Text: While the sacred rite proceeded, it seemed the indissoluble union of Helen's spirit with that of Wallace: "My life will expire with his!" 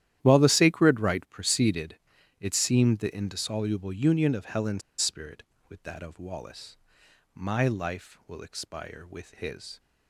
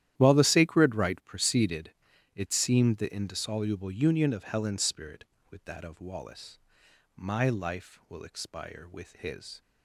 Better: second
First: starts louder than the rest; strong; until 1.2 s; 12 dB // pauses between "Helen's" and "spirit"; slight; at 4.8 s; 0.19 s long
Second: starts louder than the rest; strong; until 1.1 s; 12 dB

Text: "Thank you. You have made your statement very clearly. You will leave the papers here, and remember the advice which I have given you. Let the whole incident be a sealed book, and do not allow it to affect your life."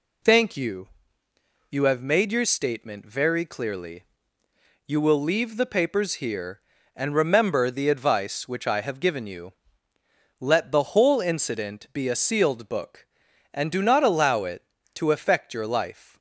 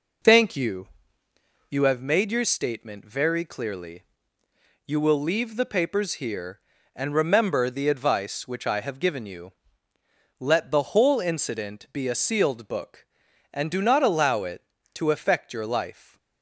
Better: first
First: none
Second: starts louder than the rest; noticeable; until 2.0 s; 4 dB

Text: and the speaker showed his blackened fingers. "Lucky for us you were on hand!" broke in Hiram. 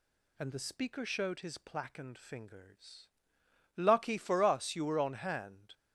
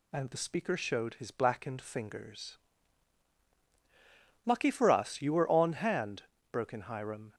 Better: second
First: stops before "broke in Hiram"; at 5.7 s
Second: none

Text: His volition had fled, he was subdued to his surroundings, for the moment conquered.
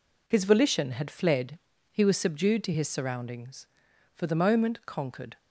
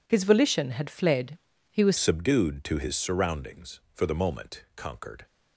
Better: first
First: none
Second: changes voice at "subdued"; from 1.9 s on; 3.3 s long

